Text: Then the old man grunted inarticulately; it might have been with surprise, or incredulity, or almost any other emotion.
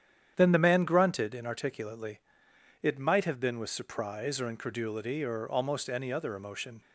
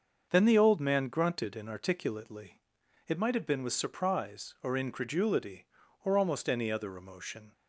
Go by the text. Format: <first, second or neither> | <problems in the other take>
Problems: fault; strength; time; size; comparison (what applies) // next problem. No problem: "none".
second | starts louder than the rest; strong; until 1.3 s; 9.5 dB; also in the second // skips "old"; at 0.5 s